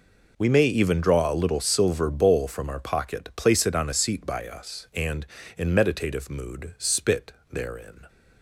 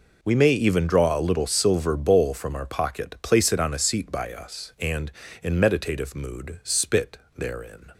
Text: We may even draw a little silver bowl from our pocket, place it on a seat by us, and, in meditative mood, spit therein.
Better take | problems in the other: neither | pauses between "spit" and "therein"; slight; the same in both

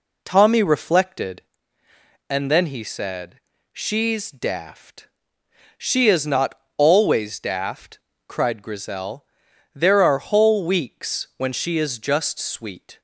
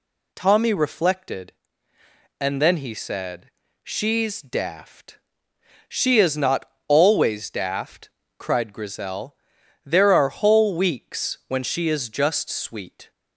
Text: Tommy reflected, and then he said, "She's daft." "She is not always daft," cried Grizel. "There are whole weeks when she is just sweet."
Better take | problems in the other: second | starts louder than the rest; slight; until 1.7 s; 3 dB // pauses between "not" and "always"; slight; at 6.5 s; 0.24 s long; slight in the second

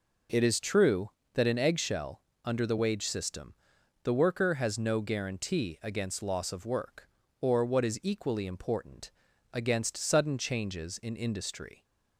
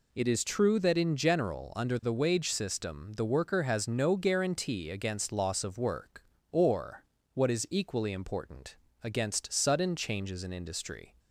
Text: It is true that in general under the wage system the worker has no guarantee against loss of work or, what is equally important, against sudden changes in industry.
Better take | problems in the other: second | says "eggshell" for "general"; at 1.5 s // pauses between "system" and "the"; noticeable; at 3.5 s; 0.48 s long

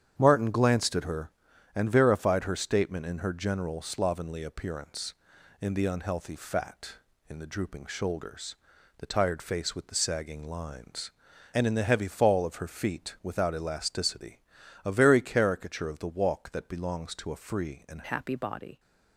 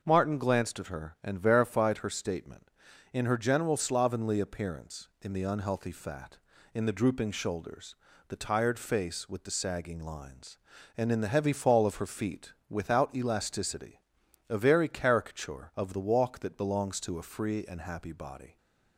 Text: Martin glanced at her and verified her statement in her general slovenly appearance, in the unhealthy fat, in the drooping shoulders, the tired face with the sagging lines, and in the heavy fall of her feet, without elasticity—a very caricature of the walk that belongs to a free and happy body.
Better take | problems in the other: second | starts louder than the rest; strong; until 1.2 s; 9 dB // changes voice at "happy"; from 18.0 s on; 0.7 s long

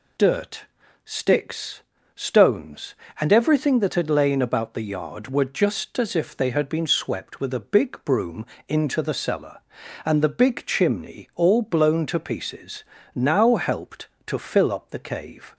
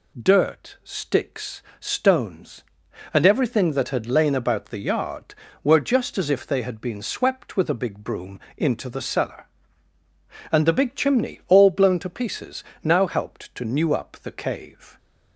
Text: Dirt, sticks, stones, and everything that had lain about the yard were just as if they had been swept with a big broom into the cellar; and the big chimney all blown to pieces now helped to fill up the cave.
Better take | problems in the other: first | pauses between "broom" and "into"; slight; at 8.3 s; 0.20 s long; slight in the first // pauses between "pieces" and "now"; slight; at 12.6 s; 0.22 s long; slight in the first // says "new" for "fill"; at 13.6 s

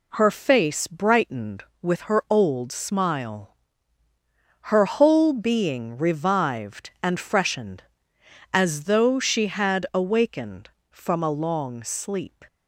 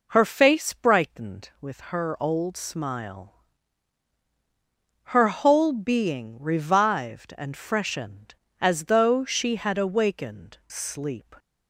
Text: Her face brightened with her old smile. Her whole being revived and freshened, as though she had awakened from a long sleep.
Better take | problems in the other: first | skips "from a long"; at 10.6 s

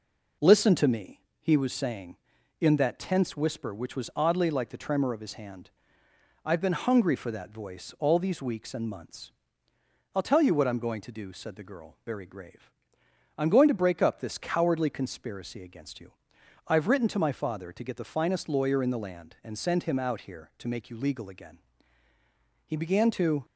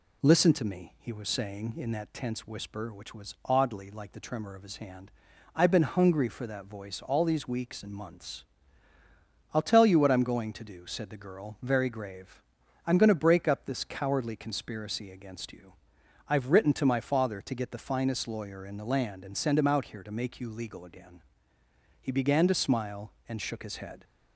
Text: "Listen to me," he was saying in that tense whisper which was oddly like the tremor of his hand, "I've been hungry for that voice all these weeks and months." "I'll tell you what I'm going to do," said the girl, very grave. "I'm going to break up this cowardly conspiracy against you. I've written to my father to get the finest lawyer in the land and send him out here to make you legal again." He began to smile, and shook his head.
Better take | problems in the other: second | stops before "smile and shook his head"; at 23.4 s

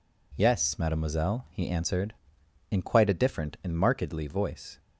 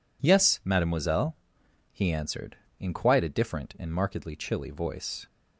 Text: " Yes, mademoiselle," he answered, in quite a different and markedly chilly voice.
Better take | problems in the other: second | skips "chilly"; at 4.2 s

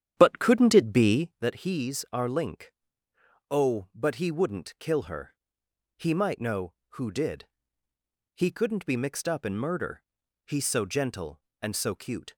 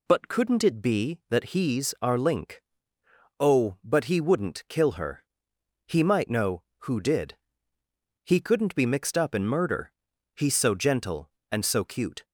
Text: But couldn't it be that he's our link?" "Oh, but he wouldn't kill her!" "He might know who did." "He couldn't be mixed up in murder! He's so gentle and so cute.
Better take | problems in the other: second | starts louder than the rest; strong; until 1.4 s; 9.5 dB

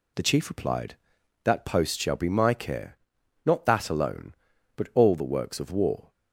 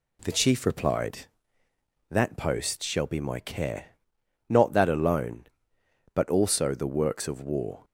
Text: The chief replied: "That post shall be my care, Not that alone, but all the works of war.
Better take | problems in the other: first | says "also" for "all"; at 6.2 s

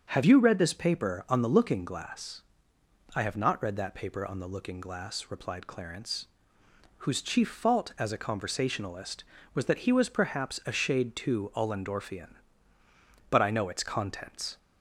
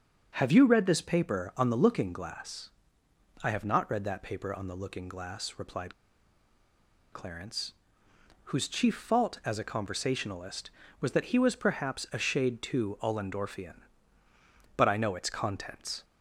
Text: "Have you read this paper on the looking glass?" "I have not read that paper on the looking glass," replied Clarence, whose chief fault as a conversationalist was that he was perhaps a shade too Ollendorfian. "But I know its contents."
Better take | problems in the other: first | starts louder than the rest; until 1.3 s; 7 dB; also in the first // pauses between "replied" and "Clarence"; at 5.9 s; 1.1 s long

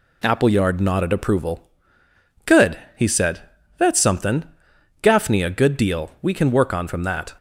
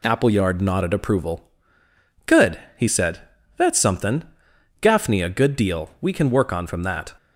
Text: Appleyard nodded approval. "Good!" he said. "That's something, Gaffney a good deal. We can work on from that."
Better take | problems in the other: neither | none

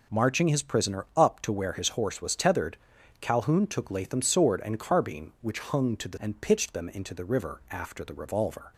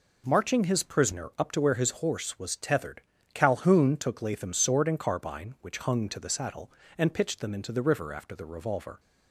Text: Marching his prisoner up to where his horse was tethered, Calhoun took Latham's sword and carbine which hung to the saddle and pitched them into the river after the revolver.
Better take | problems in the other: second | skips "saddle"; at 6.1 s

